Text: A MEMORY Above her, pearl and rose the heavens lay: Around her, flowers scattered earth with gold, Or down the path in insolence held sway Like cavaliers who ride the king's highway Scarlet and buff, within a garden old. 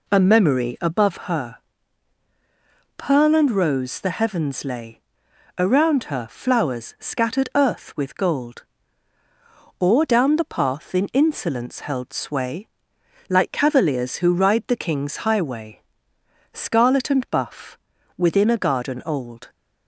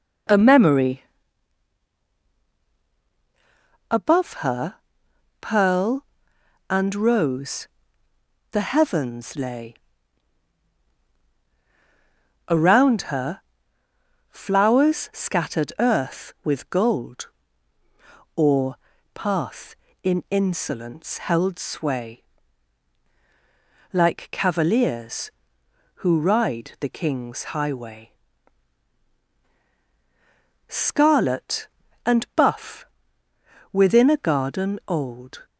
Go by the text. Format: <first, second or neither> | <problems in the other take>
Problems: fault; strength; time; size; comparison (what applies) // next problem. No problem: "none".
first | pauses between "MEMORY" and "Above"; strong; at 1.0 s; 2.8 s long // pauses between "rose" and "the"; noticeable; at 7.6 s; 0.86 s long // skips "down the"; at 18.9 s // pauses between "sway" and "Like"; strong; at 22.2 s; 1.6 s long; noticeable in the first // pauses between "highway" and "Scarlet"; strong; at 28.1 s; 2.5 s long; noticeable in the first